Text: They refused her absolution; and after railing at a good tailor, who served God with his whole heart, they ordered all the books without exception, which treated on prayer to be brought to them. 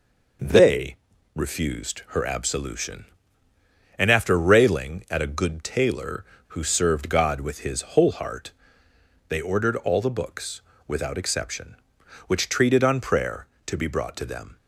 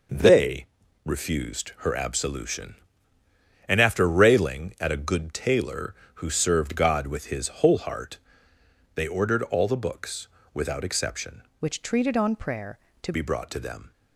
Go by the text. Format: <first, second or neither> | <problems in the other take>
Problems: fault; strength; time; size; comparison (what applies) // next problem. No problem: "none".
first | pauses between "They" and "refused"; at 0.6 s; 0.40 s long; also in the first // pauses between "his" and "whole"; slight; at 7.4 s; 0.16 s long; slight in the first // pauses between "books" and "without"; slight; at 10.2 s; 0.26 s long; slight in the first // changes voice from "which" to "to"; from 11.6 to 13.1 s; 1.5 s long